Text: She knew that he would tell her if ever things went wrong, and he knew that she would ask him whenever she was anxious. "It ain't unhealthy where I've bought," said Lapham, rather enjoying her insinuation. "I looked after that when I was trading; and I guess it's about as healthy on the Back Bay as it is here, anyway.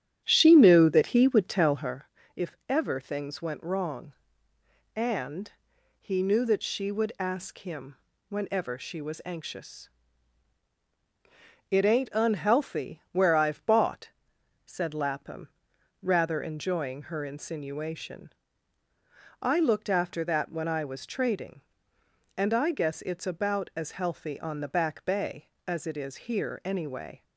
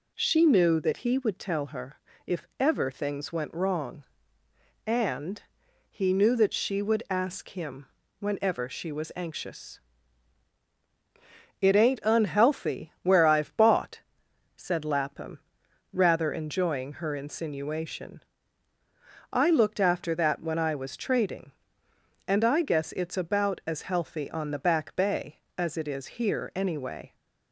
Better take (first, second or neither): second